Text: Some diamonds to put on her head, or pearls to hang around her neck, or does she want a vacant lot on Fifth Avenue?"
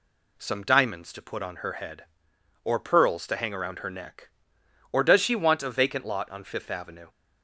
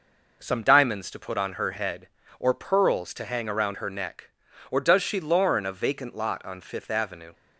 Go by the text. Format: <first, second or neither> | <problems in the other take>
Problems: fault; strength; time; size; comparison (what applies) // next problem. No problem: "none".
first | says "lorn" for "want"; at 5.1 s